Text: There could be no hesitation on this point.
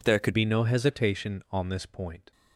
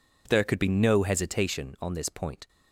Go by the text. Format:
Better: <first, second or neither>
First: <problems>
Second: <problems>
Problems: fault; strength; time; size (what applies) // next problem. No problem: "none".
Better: second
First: changes voice at "be"; from 0.3 s on; 2.0 s long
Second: none